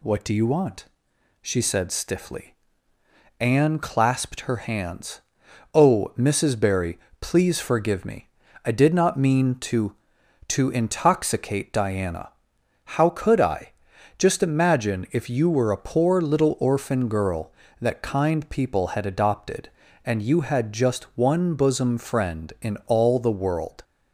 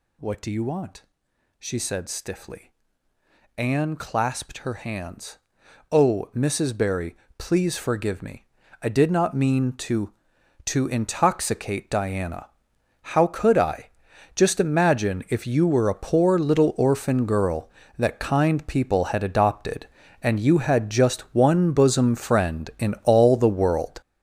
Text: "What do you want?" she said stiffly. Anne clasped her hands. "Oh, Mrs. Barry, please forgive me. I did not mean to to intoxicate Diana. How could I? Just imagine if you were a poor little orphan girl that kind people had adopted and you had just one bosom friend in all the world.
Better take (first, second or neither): first